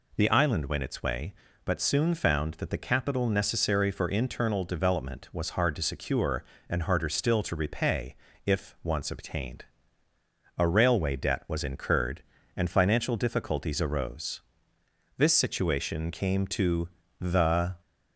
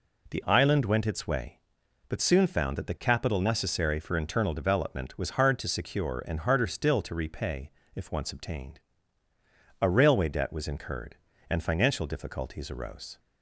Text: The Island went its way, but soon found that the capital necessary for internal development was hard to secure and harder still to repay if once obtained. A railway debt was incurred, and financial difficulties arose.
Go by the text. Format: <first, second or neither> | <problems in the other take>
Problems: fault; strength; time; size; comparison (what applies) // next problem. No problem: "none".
second | pauses between "repay" and "if"; slight; at 8.1 s; 0.30 s long; slight in the second // goes on to say "This situation came to the"; strong; from 15.1 s on; 2.5 s long